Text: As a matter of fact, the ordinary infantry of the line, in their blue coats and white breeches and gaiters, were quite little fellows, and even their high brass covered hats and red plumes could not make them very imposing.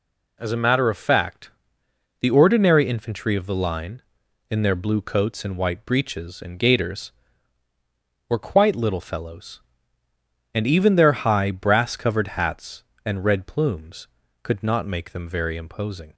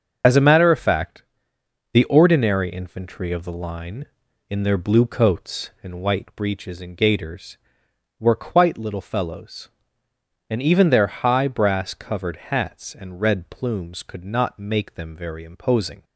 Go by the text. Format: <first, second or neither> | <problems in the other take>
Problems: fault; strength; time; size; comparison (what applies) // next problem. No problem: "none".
first | loses the start of "As"; at 0.2 s; 30 ms // starts louder than the rest; until 1.9 s; 6.5 dB